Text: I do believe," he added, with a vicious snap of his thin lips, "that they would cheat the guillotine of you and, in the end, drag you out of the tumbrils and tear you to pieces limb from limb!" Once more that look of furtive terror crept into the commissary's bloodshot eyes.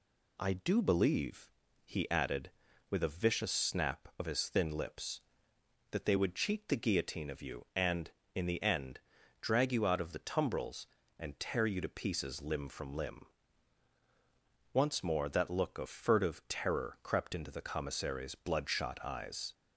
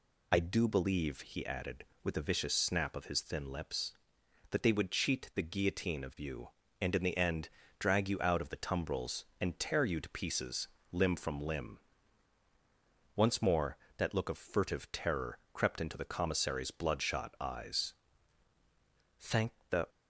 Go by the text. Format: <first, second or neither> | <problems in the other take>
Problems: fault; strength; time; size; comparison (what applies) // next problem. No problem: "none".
first | pauses between "pieces" and "limb"; slight; at 10.6 s; 0.24 s long // pauses between "terror" and "crept"; slight; at 15.3 s; 0.16 s long // goes on to say "Thank the"; noticeable; from 19.1 s on; 0.70 s long